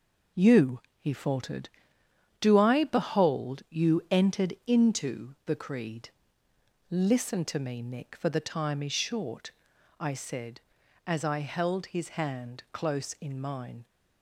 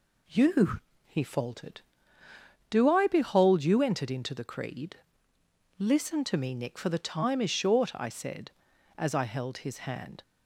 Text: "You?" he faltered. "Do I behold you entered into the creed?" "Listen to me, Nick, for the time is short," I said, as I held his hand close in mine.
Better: first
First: none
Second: stops before "close in mine"; at 10.2 s

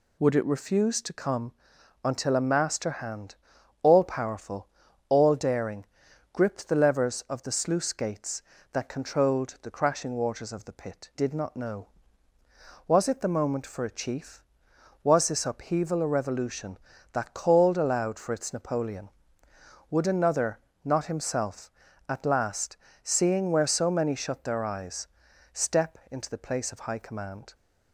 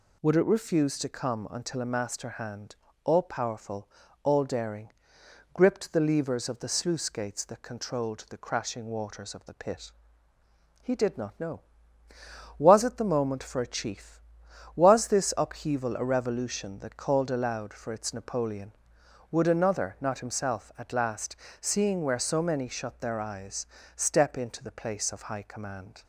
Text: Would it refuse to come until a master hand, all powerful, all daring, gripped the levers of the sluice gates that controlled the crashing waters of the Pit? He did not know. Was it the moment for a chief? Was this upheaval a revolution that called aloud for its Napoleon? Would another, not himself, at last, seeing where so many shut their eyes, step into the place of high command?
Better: second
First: pauses between "come" and "until"; noticeable; at 1.5 s; 0.52 s long // skips "He"; at 11.1 s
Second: none

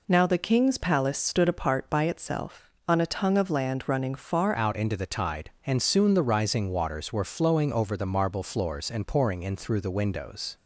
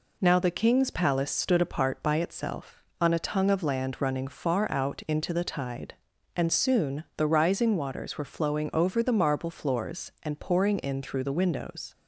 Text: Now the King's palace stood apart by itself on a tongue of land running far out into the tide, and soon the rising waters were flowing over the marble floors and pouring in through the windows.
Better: second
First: changes voice at "out"; from 4.5 s on; 6.0 s long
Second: none

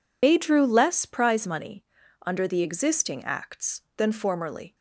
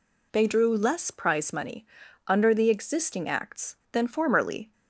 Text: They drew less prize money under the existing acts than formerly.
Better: second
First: loses the start of "They"; at 0.2 s; 40 ms // pauses between "money" and "under"; at 1.8 s; 0.42 s long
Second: pauses between "money" and "under"; at 1.8 s; 0.42 s long

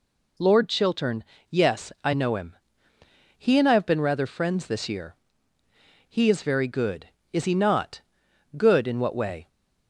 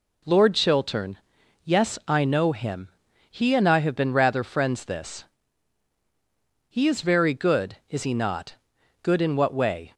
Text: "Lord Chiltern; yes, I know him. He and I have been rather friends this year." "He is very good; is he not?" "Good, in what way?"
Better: first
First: none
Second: skips "year"; at 5.9 s

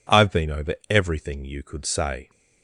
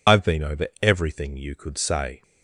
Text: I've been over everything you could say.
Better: first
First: pauses between "over" and "everything"; slight; at 0.7 s; 0.16 s long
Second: loses the start of "I've"; at 0.0 s; 80 ms // pauses between "over" and "everything"; slight; at 0.6 s; 0.16 s long

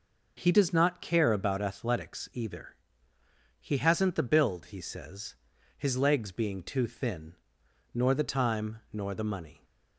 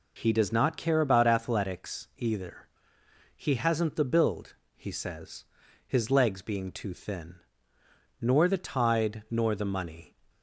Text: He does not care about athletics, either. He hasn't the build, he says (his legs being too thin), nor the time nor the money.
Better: first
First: none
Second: says "tide" for "time"; at 8.5 s

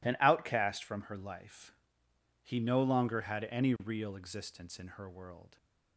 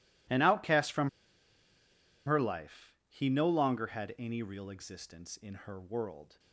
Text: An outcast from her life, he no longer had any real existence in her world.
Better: first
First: none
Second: pauses between "from" and "her"; at 1.0 s; 1.1 s long

